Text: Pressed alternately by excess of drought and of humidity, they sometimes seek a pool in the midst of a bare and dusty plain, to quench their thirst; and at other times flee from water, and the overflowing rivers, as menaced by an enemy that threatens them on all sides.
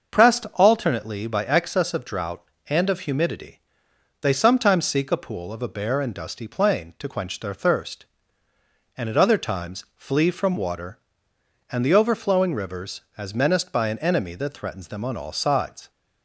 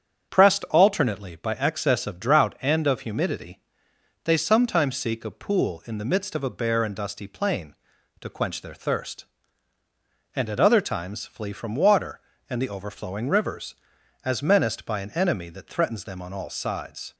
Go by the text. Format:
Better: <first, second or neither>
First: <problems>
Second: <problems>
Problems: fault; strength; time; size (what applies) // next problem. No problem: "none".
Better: second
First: starts louder than the rest; until 1.2 s; 6.5 dB // skips "in the midst"; at 5.5 s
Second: starts louder than the rest; strong; until 1.3 s; 7.5 dB